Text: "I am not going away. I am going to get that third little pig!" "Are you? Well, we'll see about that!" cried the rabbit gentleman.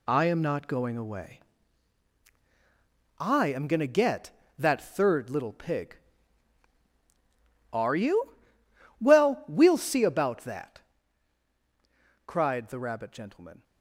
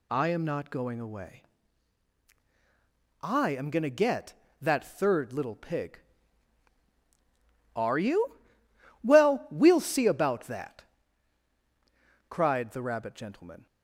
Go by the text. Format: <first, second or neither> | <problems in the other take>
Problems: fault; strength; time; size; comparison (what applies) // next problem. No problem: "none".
second | gets quieter; strong; throughout; 7.5 dB